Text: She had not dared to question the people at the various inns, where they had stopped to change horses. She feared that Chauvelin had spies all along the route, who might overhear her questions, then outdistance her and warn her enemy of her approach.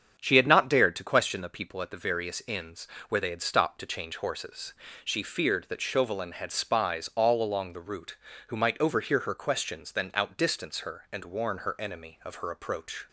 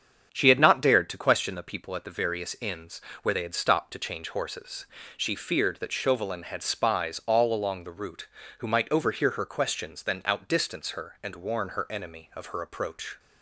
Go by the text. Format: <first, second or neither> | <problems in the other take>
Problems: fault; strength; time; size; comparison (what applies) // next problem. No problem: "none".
neither | starts louder than the rest; strong; the same in both